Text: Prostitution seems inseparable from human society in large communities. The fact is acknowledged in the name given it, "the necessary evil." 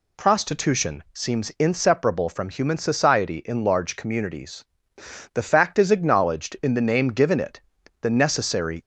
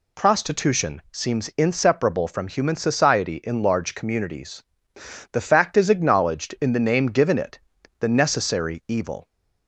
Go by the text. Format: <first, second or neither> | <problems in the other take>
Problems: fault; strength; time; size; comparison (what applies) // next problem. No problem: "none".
second | stops before "evil"; at 8.8 s